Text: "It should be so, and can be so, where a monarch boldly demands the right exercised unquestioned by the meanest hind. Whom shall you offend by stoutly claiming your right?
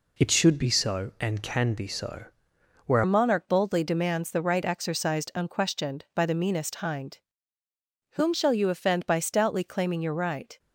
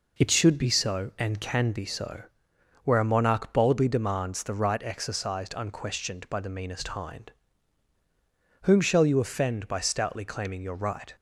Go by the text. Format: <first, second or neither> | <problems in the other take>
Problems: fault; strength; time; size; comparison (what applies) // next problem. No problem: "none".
second | changes voice at "a"; from 3.0 s on; 7.5 s long